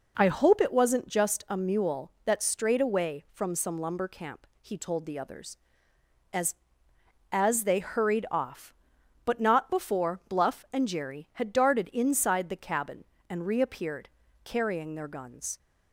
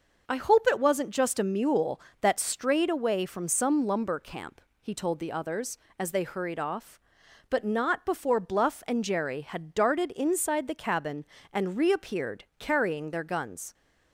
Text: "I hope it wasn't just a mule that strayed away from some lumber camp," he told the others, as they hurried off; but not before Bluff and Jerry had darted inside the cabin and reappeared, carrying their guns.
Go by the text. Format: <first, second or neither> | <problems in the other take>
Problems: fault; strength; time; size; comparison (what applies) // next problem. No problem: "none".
second | says "as" twice; at 7.2 s